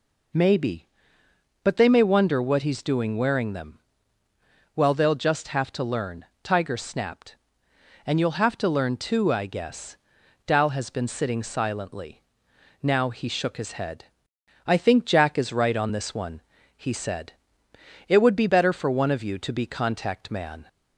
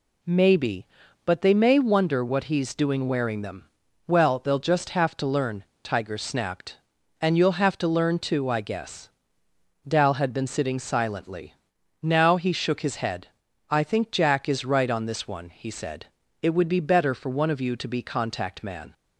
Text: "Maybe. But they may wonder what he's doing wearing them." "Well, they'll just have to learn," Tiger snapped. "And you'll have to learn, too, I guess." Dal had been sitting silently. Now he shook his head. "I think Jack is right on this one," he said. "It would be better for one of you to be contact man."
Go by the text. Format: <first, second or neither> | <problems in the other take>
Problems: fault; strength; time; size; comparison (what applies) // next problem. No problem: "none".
second | says "has" for "had"; at 10.6 s